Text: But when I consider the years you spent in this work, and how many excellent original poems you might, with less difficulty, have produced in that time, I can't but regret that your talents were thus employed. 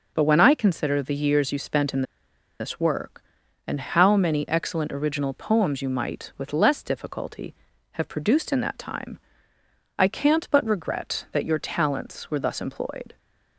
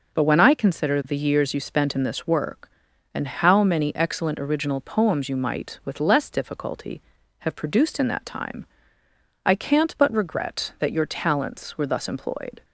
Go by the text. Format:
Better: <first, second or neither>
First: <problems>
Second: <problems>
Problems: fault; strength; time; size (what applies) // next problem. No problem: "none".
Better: second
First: pauses between "in" and "this"; noticeable; at 2.0 s; 0.57 s long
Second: none